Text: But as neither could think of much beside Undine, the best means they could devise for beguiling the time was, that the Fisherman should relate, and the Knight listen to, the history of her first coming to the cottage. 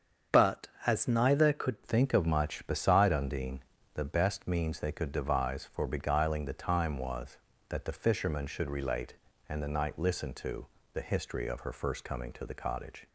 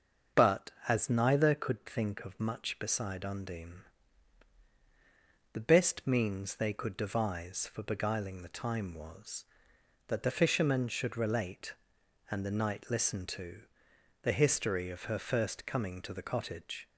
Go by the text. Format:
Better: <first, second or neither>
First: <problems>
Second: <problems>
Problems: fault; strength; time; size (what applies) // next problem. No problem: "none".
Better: second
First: starts louder than the rest; strong; until 1.4 s; 7.5 dB // changes voice at "think"; from 1.8 s on; 11.2 s long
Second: starts louder than the rest; until 1.5 s; 6.5 dB